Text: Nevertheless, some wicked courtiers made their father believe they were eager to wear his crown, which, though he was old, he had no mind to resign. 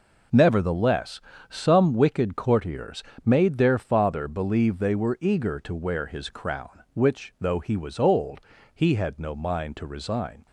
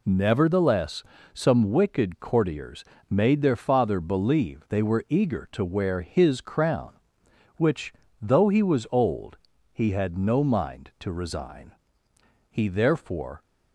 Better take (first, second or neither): first